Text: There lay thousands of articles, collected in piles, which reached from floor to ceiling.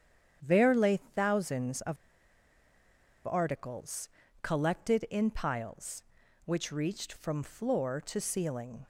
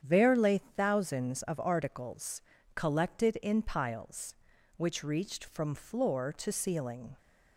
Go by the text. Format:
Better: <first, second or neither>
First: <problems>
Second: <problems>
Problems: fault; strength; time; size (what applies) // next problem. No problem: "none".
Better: second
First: starts louder than the rest; strong; until 1.4 s; 8.5 dB // pauses between "of" and "articles"; strong; at 1.9 s; 1.3 s long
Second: starts louder than the rest; strong; until 1.0 s; 8.5 dB